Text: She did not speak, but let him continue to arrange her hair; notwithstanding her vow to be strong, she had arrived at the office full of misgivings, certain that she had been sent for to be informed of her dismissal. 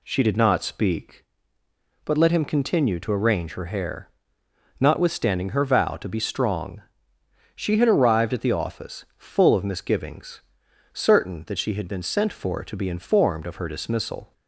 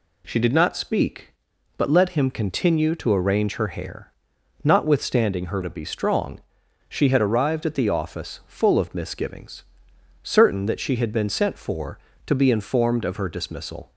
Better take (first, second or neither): first